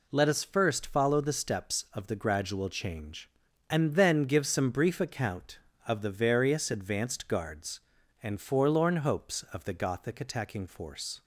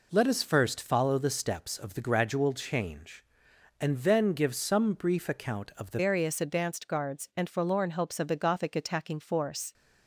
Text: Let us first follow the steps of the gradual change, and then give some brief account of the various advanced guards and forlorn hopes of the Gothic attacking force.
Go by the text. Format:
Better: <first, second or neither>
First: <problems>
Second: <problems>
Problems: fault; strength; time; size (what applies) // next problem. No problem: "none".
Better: first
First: none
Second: changes voice at "various"; from 6.0 s on; 3.7 s long